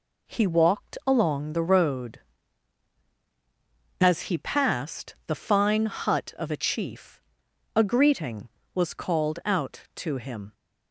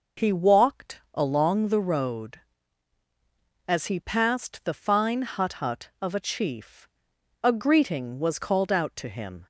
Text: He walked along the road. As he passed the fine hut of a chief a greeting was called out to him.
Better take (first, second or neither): first